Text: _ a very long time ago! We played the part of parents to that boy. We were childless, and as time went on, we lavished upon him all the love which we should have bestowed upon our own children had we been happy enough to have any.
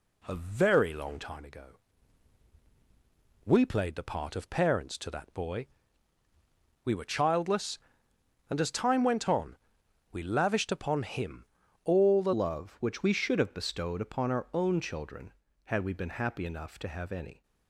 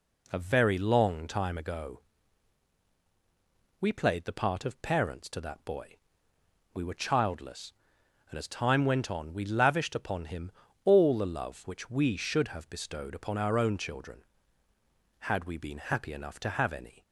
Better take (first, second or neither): second